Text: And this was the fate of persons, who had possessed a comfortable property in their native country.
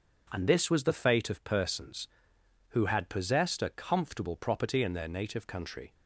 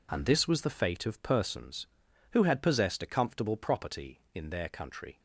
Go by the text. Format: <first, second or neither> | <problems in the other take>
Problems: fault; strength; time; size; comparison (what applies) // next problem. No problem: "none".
first | skips "native"; at 4.6 s